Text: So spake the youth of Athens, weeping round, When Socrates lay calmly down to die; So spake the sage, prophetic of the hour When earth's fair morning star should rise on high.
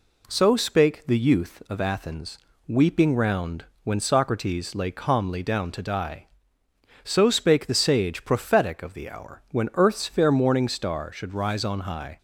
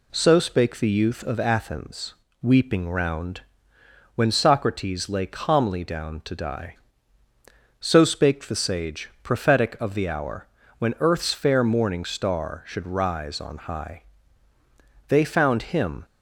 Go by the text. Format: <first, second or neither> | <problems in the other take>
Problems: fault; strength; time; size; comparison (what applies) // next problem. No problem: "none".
first | pauses between "hour" and "When"; slight; at 10.4 s; 0.32 s long // goes on to say "They found Him"; noticeable; from 15.0 s on; 0.98 s long